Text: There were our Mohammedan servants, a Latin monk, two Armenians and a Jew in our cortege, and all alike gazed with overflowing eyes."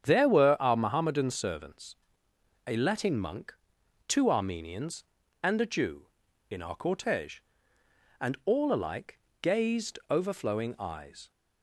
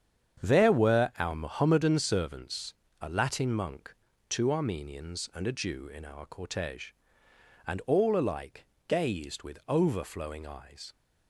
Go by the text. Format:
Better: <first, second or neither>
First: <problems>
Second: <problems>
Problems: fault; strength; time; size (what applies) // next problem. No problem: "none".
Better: second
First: starts louder than the rest; strong; until 1.0 s; 8.5 dB // pauses between "alike" and "gazed"; slight; at 9.1 s; 0.22 s long // skips "with"; at 10.0 s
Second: starts louder than the rest; strong; until 1.5 s; 8 dB // pauses between "alike" and "gazed"; slight; at 8.6 s; 0.22 s long